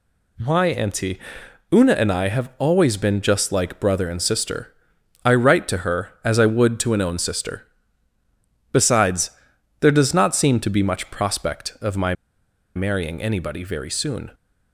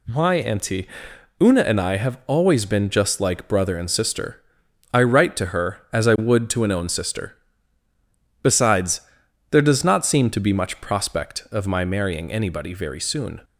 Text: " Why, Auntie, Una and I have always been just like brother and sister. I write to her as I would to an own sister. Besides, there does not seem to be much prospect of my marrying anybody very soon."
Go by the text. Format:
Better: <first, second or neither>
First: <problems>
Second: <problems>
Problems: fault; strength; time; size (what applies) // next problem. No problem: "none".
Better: second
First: pauses between "my" and "marrying"; noticeable; at 12.1 s; 0.62 s long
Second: none